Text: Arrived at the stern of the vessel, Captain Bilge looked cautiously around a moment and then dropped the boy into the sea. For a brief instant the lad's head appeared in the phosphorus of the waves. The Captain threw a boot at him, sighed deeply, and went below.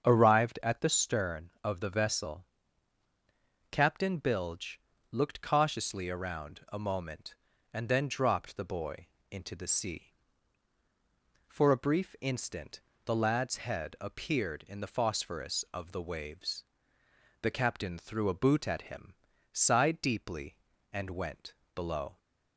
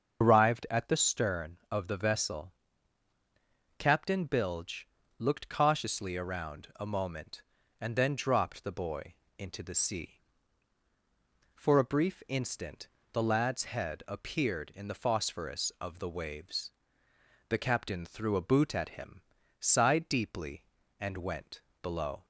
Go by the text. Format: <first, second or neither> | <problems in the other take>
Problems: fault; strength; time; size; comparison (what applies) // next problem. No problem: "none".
first | loses the start of "Arrived"; at 0.2 s; 90 ms // starts louder than the rest; until 1.2 s; 6.5 dB; strong in the first // pauses between "Bilge" and "looked"; slight; at 4.8 s; 0.32 s long; slight in the first // pauses between "boy" and "into"; slight; at 9.1 s; 0.24 s long; slight in the first // pauses between "instant" and "the"; slight; at 12.8 s; 0.26 s long; slight in the first // pauses between "went" and "below"; slight; at 21.6 s; 0.20 s long; slight in the first